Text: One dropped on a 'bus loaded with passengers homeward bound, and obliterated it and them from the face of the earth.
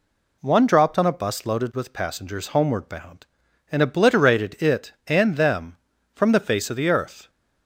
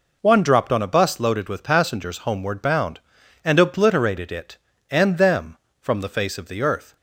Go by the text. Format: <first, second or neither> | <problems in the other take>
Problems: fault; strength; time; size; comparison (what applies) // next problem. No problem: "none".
neither | none